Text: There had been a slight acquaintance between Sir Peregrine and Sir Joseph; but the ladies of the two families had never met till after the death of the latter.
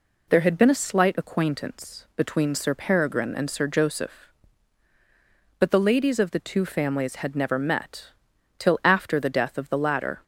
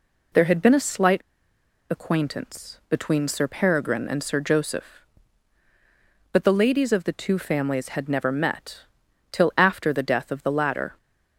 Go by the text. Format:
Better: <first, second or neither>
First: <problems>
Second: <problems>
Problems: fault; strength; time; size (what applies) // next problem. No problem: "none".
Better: first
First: pauses between "met" and "till"; noticeable; at 8.0 s; 0.48 s long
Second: pauses between "slight" and "acquaintance"; noticeable; at 1.2 s; 0.68 s long // pauses between "met" and "till"; noticeable; at 8.8 s; 0.48 s long